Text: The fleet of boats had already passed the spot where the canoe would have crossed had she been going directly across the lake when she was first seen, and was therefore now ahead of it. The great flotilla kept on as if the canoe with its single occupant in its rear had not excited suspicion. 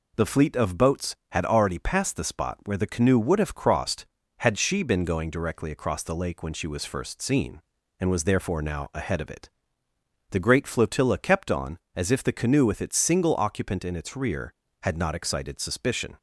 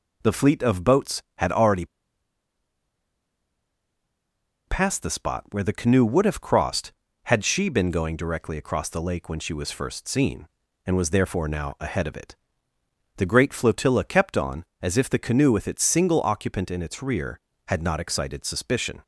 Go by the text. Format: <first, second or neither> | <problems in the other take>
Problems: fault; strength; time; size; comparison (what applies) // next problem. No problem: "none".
first | pauses between "already" and "passed"; strong; at 1.8 s; 2.8 s long